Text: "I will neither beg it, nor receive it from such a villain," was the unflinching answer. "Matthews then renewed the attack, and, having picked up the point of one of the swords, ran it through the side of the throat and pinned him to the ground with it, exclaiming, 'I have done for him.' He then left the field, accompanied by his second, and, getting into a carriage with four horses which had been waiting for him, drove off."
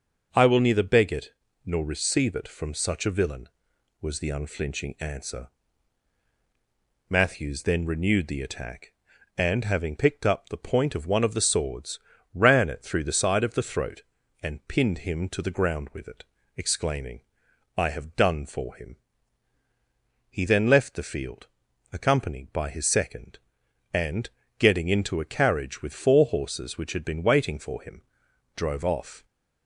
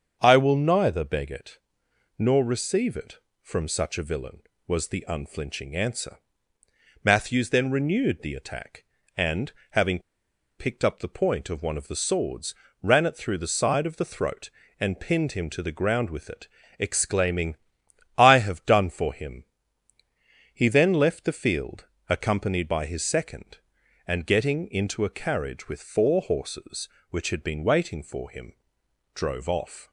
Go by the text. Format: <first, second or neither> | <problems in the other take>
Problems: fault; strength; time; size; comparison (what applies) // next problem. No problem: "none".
first | starts louder than the rest; until 1.2 s; 7 dB; noticeable in the first // pauses between "having" and "picked"; noticeable; at 9.9 s; 0.59 s long